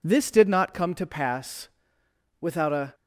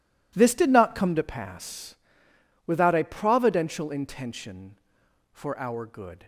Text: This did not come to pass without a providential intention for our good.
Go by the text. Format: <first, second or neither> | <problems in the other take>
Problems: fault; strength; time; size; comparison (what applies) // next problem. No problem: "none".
second | pauses between "pass" and "without"; noticeable; at 1.6 s; 0.72 s long; noticeable in the second // stops before "providential intention for our good"; at 2.9 s